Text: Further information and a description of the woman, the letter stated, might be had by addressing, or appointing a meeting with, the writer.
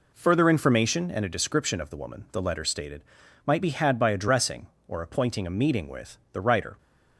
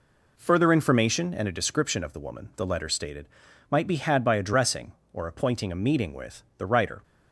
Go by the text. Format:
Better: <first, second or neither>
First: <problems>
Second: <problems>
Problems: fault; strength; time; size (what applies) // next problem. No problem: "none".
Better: neither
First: none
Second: none